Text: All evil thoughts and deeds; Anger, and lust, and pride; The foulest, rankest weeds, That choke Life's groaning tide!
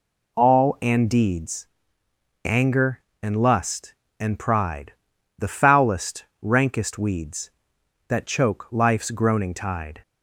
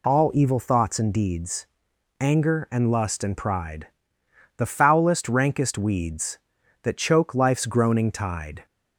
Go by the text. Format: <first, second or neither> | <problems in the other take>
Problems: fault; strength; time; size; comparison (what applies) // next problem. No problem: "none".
second | skips "evil thoughts"; at 0.7 s